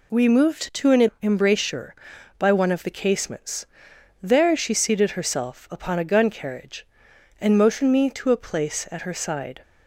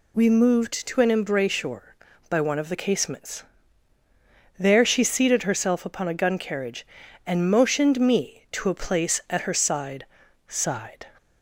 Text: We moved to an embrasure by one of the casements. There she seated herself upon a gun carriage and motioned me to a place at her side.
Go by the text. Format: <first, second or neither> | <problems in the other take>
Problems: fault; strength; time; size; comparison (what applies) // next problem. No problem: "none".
first | says "side" twice; at 10.4 s